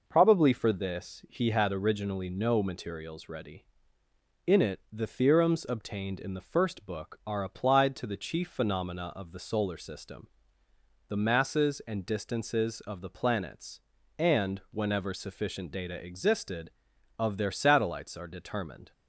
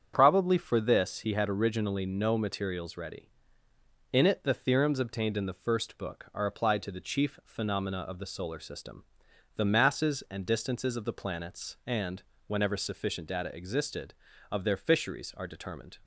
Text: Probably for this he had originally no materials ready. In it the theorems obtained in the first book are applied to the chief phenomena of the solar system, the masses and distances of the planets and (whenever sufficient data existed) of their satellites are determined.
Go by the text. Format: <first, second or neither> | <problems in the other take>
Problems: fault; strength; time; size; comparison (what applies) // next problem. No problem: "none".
first | starts louder than the rest; strong; until 1.1 s; 8 dB // says "fisheries" for "satellites"; at 14.7 s